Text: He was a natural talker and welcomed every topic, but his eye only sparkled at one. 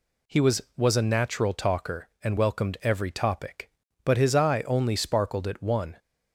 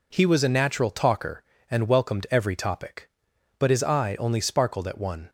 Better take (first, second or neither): second